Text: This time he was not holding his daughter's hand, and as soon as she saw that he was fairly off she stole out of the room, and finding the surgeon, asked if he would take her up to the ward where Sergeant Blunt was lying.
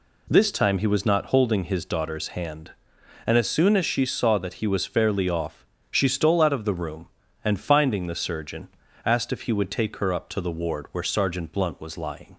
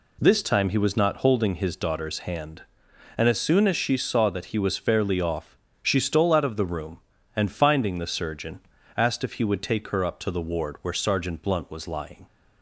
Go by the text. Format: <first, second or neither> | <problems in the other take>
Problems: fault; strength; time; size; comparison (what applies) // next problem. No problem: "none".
neither | pauses between "off" and "she"; slight; the same in both